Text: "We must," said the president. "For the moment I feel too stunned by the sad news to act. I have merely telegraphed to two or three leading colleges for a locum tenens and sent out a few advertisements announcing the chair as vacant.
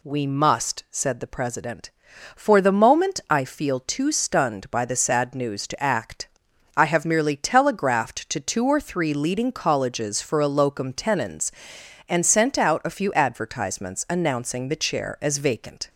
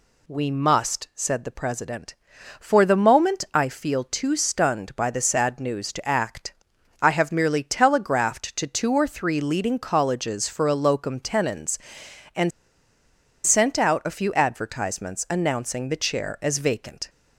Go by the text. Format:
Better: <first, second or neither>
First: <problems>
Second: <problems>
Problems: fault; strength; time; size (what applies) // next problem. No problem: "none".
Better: first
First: none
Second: pauses between "and" and "sent"; noticeable; at 12.5 s; 0.96 s long